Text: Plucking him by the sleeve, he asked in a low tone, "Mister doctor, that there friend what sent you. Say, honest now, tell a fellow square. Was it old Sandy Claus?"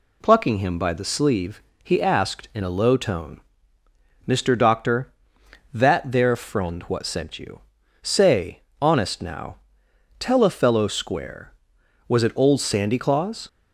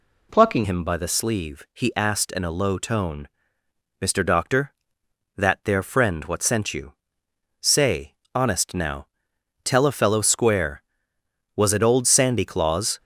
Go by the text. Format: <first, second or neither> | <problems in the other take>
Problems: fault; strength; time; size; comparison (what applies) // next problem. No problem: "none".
first | changes voice at "him"; from 0.6 s on; 12.3 s long